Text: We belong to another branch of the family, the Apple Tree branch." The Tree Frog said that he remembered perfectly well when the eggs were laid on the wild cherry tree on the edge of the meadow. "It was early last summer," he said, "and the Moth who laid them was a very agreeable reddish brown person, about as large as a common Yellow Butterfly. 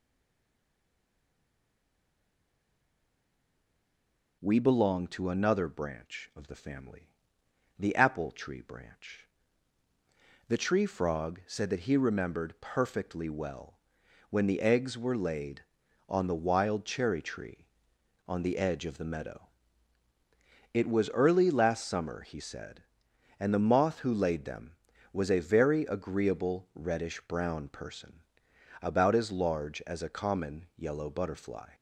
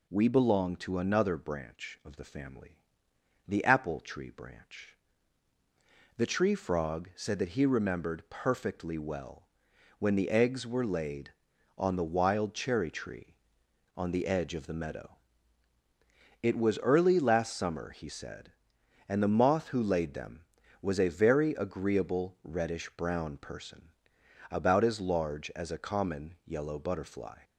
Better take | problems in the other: second | stays silent before the first word; strong; until 4.4 s; 4.4 s long // pauses between "well" and "when"; noticeable; at 13.7 s; 0.50 s long; noticeable in the second

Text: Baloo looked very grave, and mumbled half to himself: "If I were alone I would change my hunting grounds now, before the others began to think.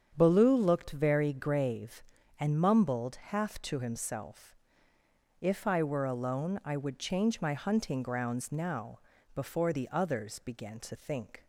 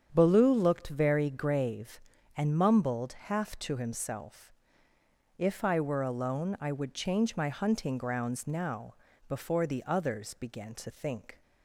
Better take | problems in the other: neither | starts louder than the rest; strong; the same in both

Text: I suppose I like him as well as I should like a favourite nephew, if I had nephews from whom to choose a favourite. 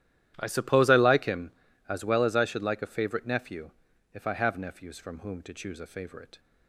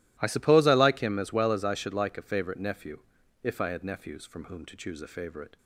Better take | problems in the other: second | starts louder than the rest; strong; until 1.3 s; 12.5 dB // says "have" for "had"; at 4.3 s

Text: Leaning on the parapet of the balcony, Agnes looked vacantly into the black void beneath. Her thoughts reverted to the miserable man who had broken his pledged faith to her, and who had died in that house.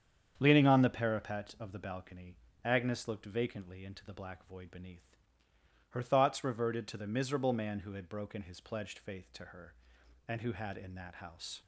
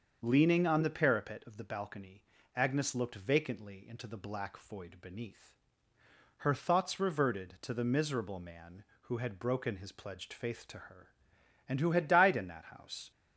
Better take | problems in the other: second | starts louder than the rest; strong; until 1.3 s; 8 dB; also in the second // skips "died"; at 10.7 s

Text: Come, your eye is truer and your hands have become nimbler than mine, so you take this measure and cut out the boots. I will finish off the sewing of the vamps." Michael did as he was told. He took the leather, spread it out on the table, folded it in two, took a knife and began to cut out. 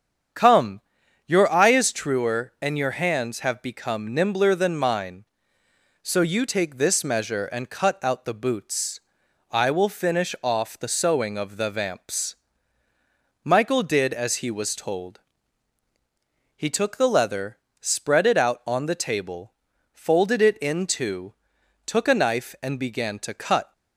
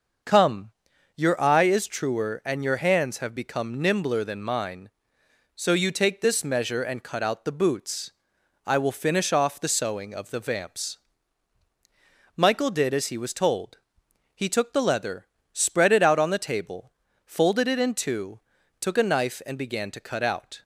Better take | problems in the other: second | starts louder than the rest; strong; until 1.8 s; 8 dB; also in the second // stops before "out"; at 23.7 s

